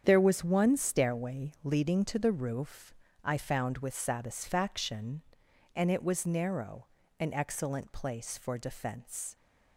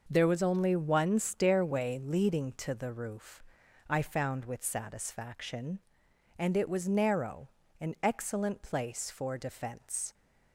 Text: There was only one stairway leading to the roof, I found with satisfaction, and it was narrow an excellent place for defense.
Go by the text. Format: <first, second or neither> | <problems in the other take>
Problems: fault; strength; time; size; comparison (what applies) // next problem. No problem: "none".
second | starts louder than the rest; strong; until 1.0 s; 8 dB // skips "only"; at 0.4 s // pauses between "narrow" and "an"; slight; at 6.8 s; 0.34 s long; slight in the second